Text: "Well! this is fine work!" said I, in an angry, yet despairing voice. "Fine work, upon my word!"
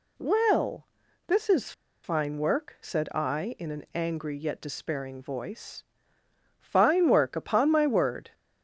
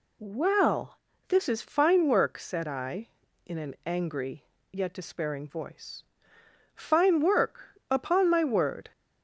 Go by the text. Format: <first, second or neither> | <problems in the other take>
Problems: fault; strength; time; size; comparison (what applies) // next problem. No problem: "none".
second | pauses between "is" and "fine"; slight; at 1.7 s; 0.31 s long